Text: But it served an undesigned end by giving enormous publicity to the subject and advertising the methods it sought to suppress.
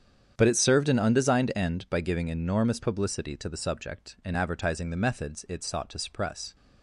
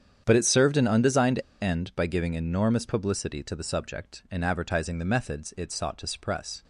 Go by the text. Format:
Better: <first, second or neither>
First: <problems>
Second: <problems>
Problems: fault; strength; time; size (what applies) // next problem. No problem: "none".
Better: first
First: starts louder than the rest; strong; until 1.3 s; 8.5 dB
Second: starts louder than the rest; strong; until 1.2 s; 8.5 dB // pauses between "undesigned" and "end"; slight; at 1.3 s; 0.23 s long